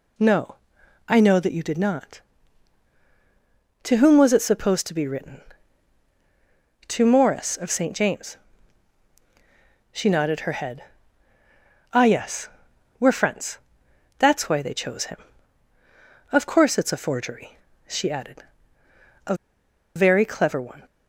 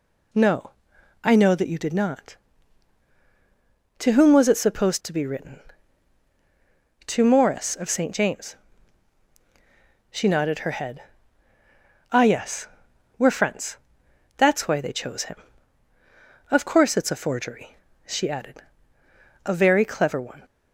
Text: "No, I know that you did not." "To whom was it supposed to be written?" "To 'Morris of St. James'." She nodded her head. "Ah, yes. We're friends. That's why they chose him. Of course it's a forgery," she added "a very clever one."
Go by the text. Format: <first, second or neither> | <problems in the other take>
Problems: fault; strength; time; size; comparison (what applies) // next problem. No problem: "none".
second | pauses between "added" and "a"; noticeable; at 18.4 s; 0.84 s long; noticeable in the second // pauses between "a" and "very"; noticeable; at 19.3 s; 0.61 s long